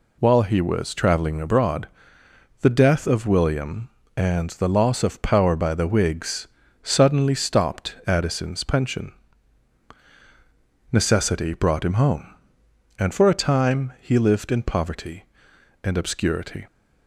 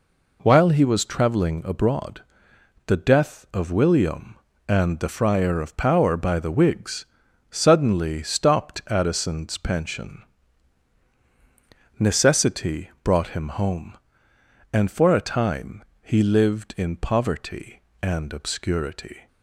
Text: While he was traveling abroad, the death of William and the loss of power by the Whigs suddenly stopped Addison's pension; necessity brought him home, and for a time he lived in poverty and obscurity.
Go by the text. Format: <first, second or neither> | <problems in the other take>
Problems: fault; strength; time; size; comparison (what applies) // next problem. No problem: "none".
first | says "friar" for "loss"; at 5.0 s // pauses between "Whigs" and "suddenly"; noticeable; at 7.0 s; 0.46 s long; slight in the first // pauses between "time" and "he"; slight; at 15.8 s; 0.18 s long